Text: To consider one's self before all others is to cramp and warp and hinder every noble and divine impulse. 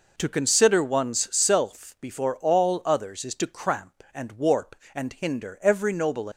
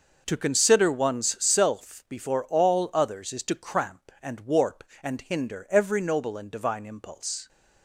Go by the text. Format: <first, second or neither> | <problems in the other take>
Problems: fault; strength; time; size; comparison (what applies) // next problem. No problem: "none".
second | stops before "and divine impulse"; at 6.3 s